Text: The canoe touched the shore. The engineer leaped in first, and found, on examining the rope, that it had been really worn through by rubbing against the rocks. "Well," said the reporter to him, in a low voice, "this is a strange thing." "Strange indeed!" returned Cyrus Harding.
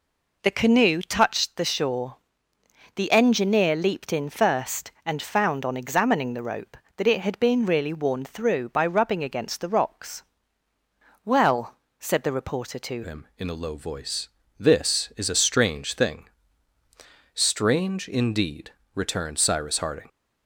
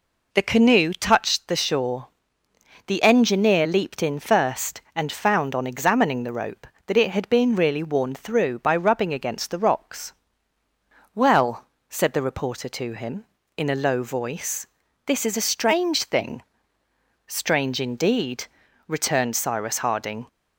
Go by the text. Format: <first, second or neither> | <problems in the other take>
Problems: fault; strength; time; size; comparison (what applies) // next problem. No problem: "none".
second | changes voice at "him"; from 13.0 s on; 7.0 s long